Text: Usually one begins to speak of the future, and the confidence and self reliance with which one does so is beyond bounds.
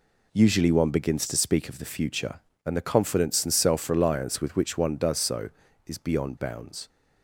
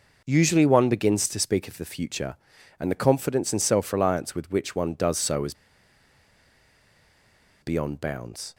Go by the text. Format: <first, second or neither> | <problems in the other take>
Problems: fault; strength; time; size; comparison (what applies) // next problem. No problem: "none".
first | pauses between "is" and "beyond"; strong; at 5.5 s; 2.0 s long